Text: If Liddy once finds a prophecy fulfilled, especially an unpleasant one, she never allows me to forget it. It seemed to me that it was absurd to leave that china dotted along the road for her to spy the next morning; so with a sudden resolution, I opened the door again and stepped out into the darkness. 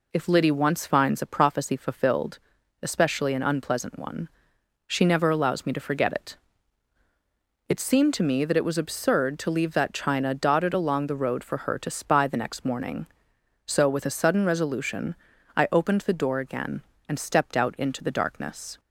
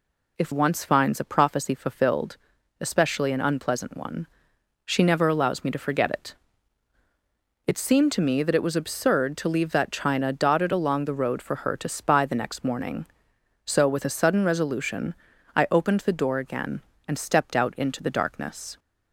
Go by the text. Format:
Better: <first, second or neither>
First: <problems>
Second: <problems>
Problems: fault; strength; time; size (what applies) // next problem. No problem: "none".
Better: first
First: none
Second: skips "Liddy"; at 0.5 s